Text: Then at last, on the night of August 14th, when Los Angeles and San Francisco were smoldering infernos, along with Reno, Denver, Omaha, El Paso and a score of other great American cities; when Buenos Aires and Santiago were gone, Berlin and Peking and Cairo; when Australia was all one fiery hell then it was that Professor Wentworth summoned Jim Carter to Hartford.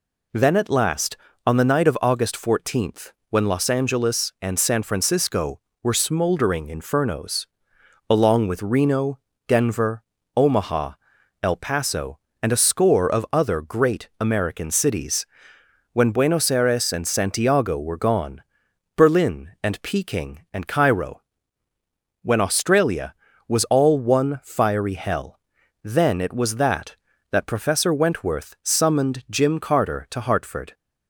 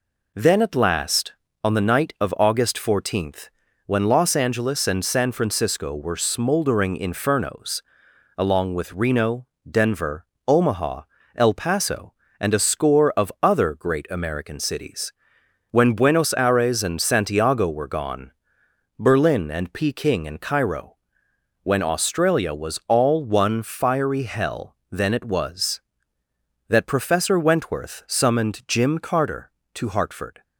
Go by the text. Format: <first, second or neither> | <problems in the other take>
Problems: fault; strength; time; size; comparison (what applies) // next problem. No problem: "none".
second | pauses between "hell" and "then"; noticeable; at 25.3 s; 0.48 s long; slight in the second // says "that" twice; at 27.3 s